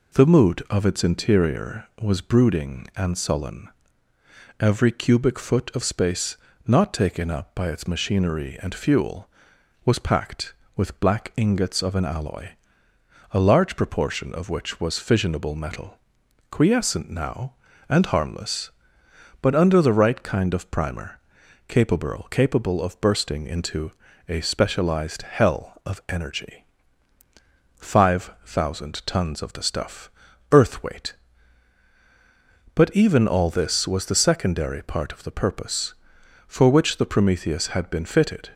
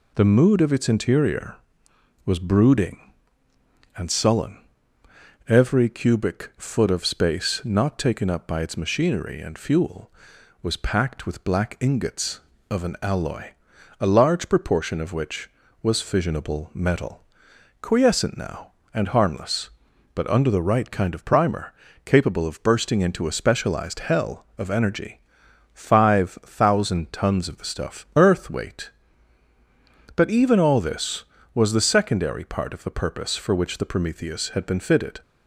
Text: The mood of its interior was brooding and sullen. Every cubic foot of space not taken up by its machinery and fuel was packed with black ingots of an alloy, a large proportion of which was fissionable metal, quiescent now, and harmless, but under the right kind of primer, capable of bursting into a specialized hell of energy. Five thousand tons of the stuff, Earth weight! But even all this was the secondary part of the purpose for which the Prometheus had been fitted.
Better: second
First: pauses between "space" and "not"; slight; at 6.3 s; 0.32 s long // says "capable" twice; at 22.2 s // pauses between "into" and "a"; slight; at 23.9 s; 0.36 s long // pauses between "Five" and "thousand"; slight; at 28.2 s; 0.16 s long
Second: none

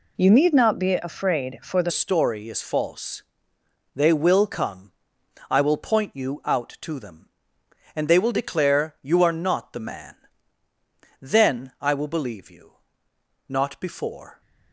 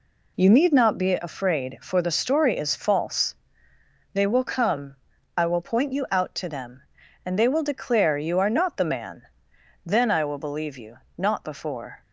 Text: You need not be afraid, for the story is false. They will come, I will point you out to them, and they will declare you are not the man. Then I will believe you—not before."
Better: second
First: changes voice at "story"; from 1.9 s on; 12.5 s long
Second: none

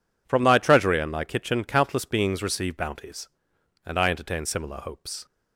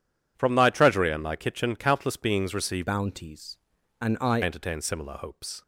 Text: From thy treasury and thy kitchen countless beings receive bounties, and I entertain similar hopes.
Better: first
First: none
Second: changes voice from "bounties" to "I"; from 2.8 to 4.4 s; 1.6 s long

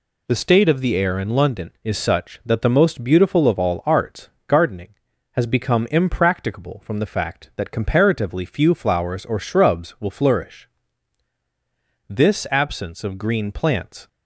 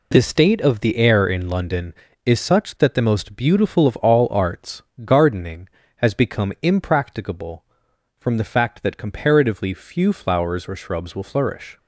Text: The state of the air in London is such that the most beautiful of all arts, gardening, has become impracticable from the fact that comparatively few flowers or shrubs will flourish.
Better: second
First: goes on to say "This absence of green plants"; strong; from 12.0 s on; 1.9 s long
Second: none

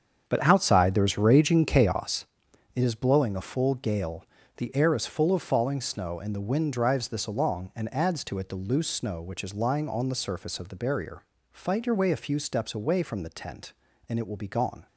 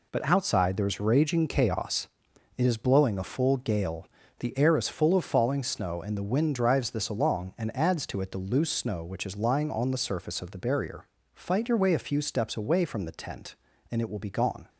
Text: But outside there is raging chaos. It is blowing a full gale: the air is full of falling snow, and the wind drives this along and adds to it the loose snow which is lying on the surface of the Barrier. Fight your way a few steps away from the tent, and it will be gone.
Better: second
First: starts louder than the rest; strong; until 2.0 s; 7.5 dB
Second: none

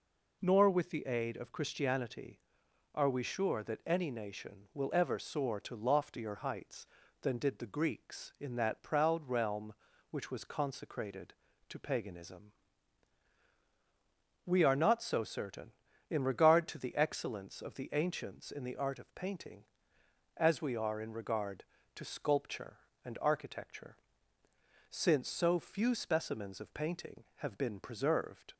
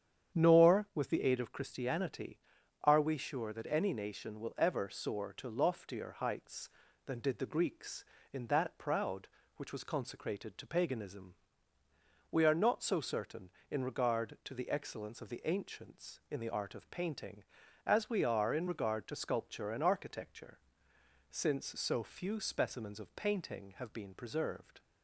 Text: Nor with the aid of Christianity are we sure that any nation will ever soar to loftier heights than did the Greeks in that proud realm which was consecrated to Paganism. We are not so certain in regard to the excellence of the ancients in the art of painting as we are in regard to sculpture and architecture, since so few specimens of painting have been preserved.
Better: first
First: none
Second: starts louder than the rest; strong; until 1.4 s; 8.5 dB // skips "realm"; at 9.4 s

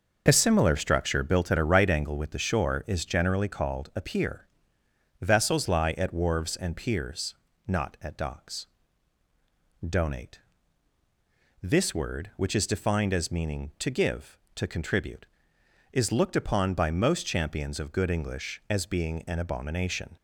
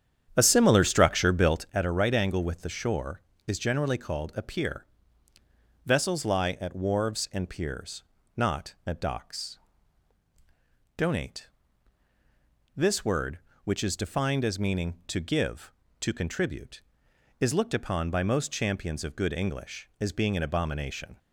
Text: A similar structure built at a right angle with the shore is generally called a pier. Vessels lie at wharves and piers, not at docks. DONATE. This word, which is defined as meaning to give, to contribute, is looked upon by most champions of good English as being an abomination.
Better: first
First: none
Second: starts louder than the rest; strong; until 1.8 s; 8.5 dB

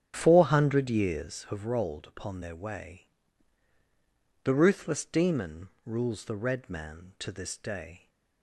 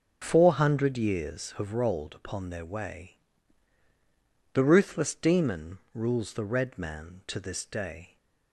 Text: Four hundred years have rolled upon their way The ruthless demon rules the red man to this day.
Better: second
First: starts louder than the rest; strong; until 1.3 s; 8.5 dB // pauses between "way" and "The"; strong; at 3.0 s; 1.3 s long // pauses between "demon" and "rules"; slight; at 5.6 s; 0.18 s long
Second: pauses between "way" and "The"; strong; at 3.1 s; 1.3 s long // pauses between "demon" and "rules"; slight; at 5.7 s; 0.17 s long

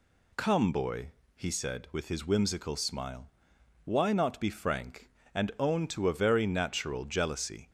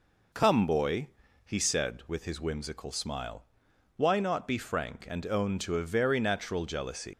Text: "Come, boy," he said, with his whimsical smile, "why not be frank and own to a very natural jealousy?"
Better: first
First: none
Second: leaves "jealousy" unfinished; at 7.1 s; 105 ms

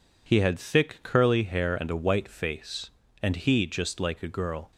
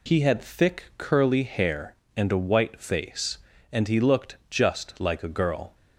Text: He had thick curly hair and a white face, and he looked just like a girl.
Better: second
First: skips "looked"; at 3.6 s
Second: none

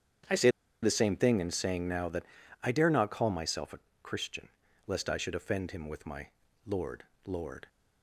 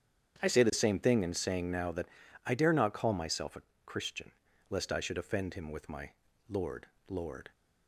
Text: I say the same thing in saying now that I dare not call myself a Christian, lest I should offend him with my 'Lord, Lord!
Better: second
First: starts louder than the rest; strong; until 1.6 s; 8.5 dB // pauses between "say" and "the"; slight; at 0.4 s; 0.34 s long // pauses between "that" and "I"; at 2.2 s; 0.40 s long // pauses between "a" and "Christian"; slight; at 3.7 s; 0.22 s long // pauses between "my" and "Lord"; at 6.2 s; 0.38 s long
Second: starts louder than the rest; strong; until 1.4 s; 8.5 dB // pauses between "that" and "I"; at 2.0 s; 0.40 s long // pauses between "a" and "Christian"; slight; at 3.6 s; 0.22 s long // pauses between "my" and "Lord"; at 6.1 s; 0.38 s long

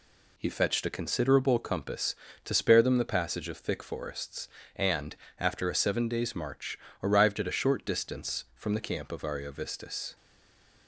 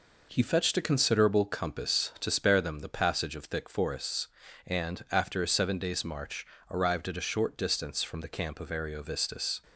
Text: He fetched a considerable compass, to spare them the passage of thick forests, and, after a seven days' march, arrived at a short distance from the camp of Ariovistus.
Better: second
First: stays silent after the last word; slight; from 10.1 s on; 0.7 s long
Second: none

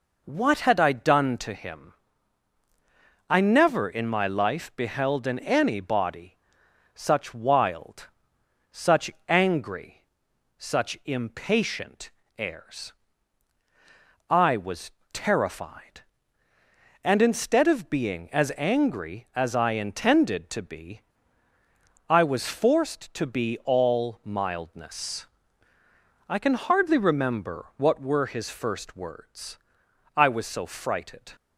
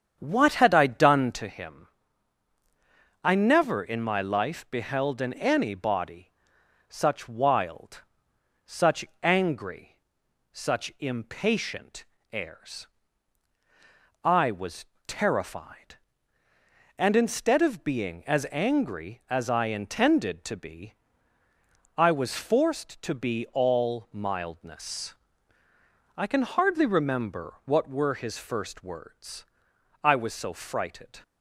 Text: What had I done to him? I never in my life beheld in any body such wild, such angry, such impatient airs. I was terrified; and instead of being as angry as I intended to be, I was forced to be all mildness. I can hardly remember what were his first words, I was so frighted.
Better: first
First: pauses between "body" and "such"; noticeable; at 6.3 s; 0.58 s long // pauses between "such" and "angry"; slight; at 9.1 s; 0.18 s long // pauses between "impatient" and "airs"; slight; at 12.0 s; 0.30 s long // pauses between "was" and "terrified"; slight; at 14.9 s; 0.22 s long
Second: starts louder than the rest; strong; until 1.5 s; 8 dB // pauses between "body" and "such"; noticeable; at 6.3 s; 0.58 s long // pauses between "such" and "angry"; slight; at 9.0 s; 0.18 s long // pauses between "impatient" and "airs"; slight; at 12.0 s; 0.30 s long // pauses between "was" and "terrified"; slight; at 14.8 s; 0.22 s long

